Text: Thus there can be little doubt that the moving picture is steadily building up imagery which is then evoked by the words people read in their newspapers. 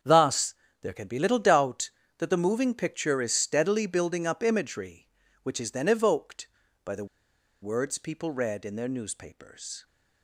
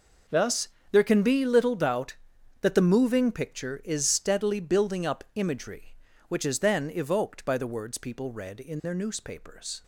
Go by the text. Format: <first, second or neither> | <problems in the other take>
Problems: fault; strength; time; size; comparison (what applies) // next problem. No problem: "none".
second | starts louder than the rest; strong; until 1.3 s; 8 dB // pauses between "Thus" and "there"; slight; at 0.5 s; 0.28 s long; slight in the second // pauses between "the" and "words"; noticeable; at 7.0 s; 0.56 s long